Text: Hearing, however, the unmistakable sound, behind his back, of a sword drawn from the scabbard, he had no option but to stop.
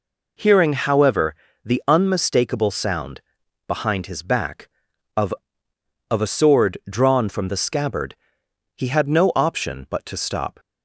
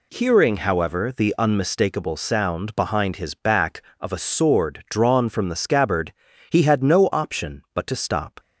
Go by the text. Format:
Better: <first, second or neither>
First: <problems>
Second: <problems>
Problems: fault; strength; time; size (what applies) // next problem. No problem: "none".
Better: second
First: says "of" twice; at 6.1 s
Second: none